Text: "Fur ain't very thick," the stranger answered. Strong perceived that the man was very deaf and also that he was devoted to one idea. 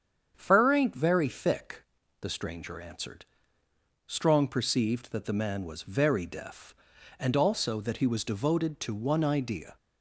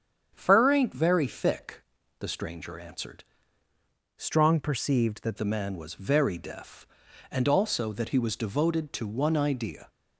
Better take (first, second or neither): first